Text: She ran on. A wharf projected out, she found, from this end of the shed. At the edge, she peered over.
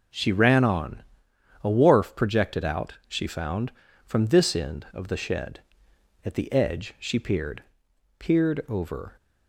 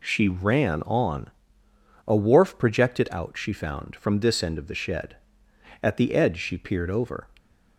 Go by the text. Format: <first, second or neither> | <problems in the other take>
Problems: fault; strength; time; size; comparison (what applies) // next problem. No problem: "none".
second | says "peered" twice; at 8.1 s